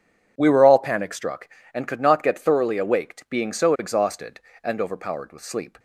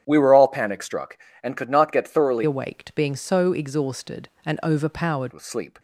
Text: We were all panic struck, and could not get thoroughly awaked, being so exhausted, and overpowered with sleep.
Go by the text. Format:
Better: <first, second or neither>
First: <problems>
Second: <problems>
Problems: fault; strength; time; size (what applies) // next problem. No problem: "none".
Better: first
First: none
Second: starts louder than the rest; strong; until 1.0 s; 9 dB // changes voice from "awaked" to "overpowered"; from 2.4 to 5.3 s; 2.9 s long